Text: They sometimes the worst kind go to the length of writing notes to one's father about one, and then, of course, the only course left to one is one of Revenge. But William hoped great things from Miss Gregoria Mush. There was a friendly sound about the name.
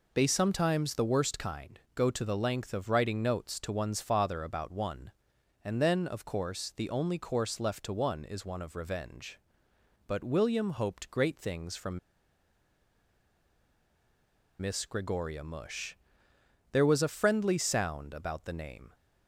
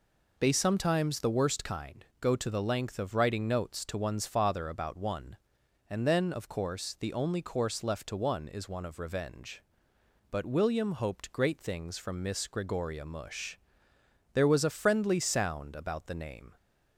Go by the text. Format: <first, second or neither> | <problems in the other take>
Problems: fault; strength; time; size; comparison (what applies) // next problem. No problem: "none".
second | pauses between "from" and "Miss"; strong; at 11.9 s; 2.6 s long